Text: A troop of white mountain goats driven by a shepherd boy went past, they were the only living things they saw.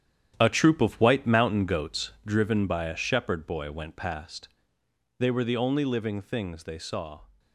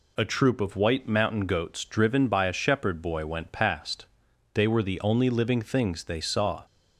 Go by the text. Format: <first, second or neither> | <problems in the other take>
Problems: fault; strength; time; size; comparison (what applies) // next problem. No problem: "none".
second | gets quieter; strong; throughout; 9 dB // pauses between "goats" and "driven"; slight; at 2.1 s; 0.16 s long